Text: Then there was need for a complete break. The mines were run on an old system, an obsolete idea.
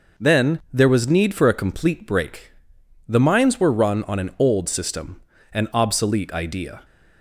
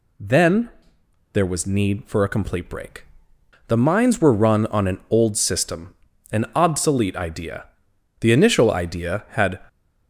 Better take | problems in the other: first | pauses between "Then" and "there"; noticeable; at 0.6 s; 0.64 s long // goes on to say "The initial idea had"; from 8.2 s on; 1.3 s long

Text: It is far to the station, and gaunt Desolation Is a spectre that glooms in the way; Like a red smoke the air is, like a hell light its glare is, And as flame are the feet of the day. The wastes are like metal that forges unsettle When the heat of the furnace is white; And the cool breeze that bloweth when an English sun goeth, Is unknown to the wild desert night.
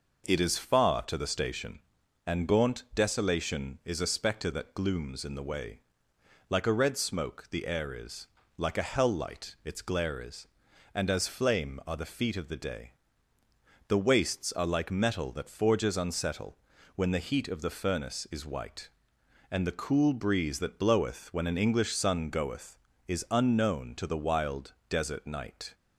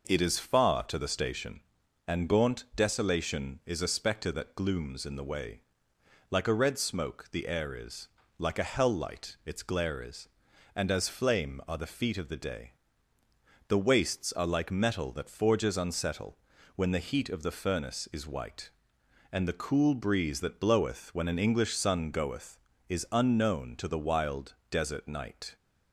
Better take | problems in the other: neither | pauses between "unsettle" and "When"; the same in both // pauses between "wild" and "desert"; slight; the same in both

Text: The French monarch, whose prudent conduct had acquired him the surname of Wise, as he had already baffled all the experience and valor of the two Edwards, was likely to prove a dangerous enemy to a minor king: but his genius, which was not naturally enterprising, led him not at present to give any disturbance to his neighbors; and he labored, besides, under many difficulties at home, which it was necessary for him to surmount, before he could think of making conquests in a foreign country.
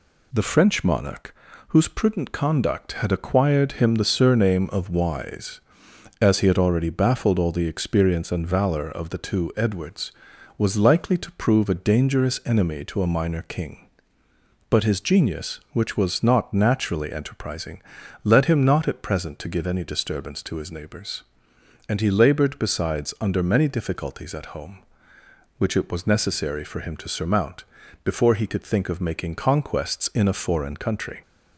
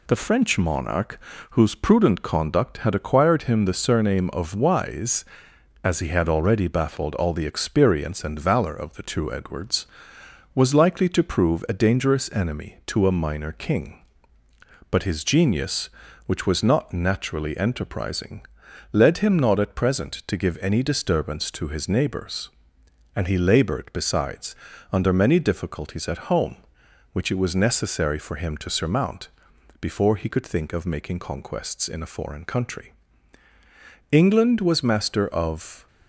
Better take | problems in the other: first | goes on to say "England was master of"; from 34.3 s on; 1.5 s long

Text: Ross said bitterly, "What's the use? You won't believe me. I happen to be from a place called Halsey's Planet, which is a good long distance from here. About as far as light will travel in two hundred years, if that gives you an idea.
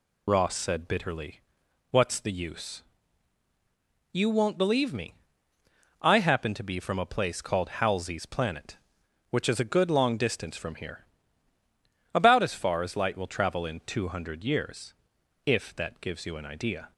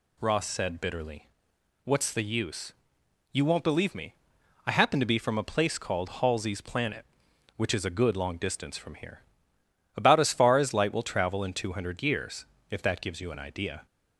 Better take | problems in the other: second | loses the start of "Ross"; at 0.2 s; 45 ms

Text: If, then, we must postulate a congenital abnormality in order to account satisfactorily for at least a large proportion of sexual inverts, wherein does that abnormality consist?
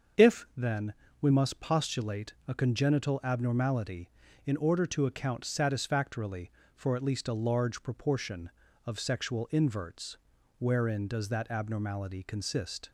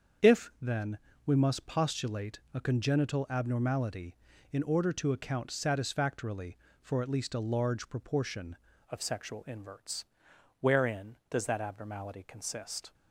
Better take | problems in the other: first | starts louder than the rest; strong; until 1.6 s; 7 dB; also in the first // changes voice at "of"; from 8.8 s on; 4.1 s long

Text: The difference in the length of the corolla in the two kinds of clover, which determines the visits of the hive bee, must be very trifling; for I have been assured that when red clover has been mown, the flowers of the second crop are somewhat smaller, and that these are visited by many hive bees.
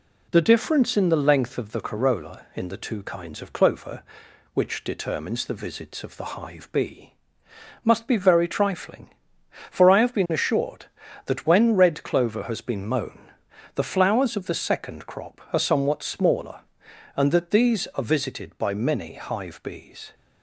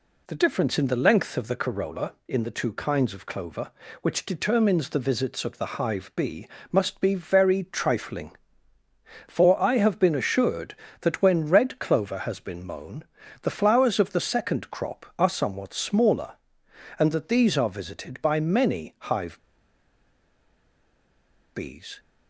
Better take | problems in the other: first | pauses between "hive" and "bees"; strong; at 19.3 s; 2.1 s long

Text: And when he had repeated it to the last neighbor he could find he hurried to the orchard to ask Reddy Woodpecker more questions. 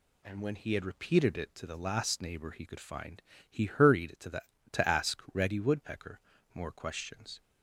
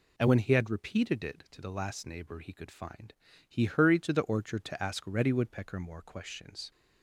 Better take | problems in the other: second | pauses between "find" and "he"; slight; at 3.2 s; 0.28 s long; slight in the second // skips "orchard"; at 4.5 s // pauses between "Woodpecker" and "more"; slight; at 6.1 s; 0.34 s long

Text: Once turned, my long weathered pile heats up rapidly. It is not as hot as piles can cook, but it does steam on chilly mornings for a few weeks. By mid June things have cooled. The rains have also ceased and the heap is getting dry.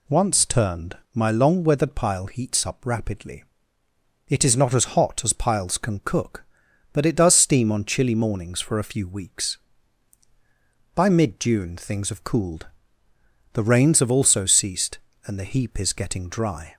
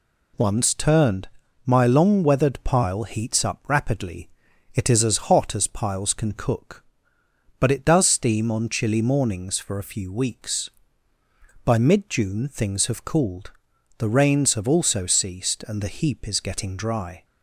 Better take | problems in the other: first | skips "not"; at 5.0 s

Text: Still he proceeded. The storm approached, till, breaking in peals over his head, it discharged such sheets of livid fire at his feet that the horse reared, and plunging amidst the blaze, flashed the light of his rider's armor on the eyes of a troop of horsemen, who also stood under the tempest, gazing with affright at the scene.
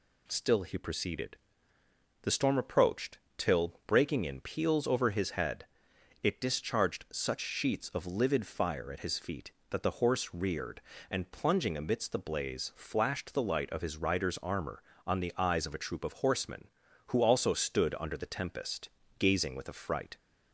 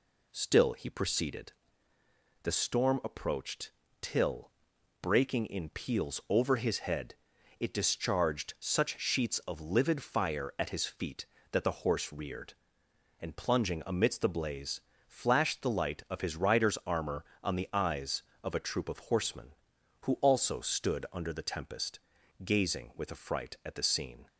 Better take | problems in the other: second | stops before "at the scene"; at 20.1 s

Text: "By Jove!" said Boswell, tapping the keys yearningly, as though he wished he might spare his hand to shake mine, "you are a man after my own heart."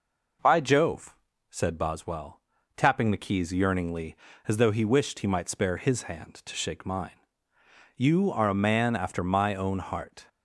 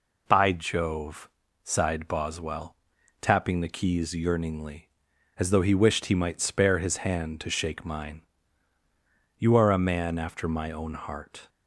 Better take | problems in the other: first | says "sighed" for "said"; at 1.6 s

